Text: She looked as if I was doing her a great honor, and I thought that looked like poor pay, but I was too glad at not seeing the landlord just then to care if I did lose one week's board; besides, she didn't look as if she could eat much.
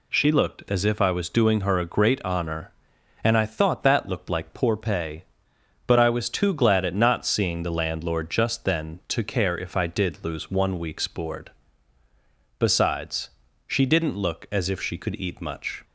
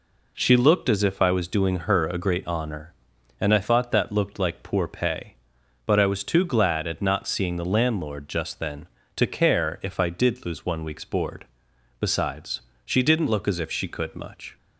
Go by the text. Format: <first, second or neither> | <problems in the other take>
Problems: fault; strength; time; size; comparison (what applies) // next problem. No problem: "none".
first | skips "eat"; at 14.1 s